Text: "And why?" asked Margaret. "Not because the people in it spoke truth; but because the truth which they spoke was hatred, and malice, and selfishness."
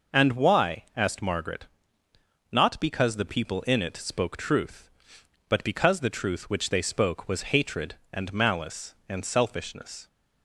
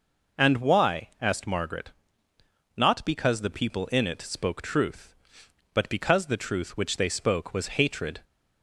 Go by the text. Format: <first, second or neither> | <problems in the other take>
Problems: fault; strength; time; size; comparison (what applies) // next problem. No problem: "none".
first | stops before "and malice and selfishness"; at 8.2 s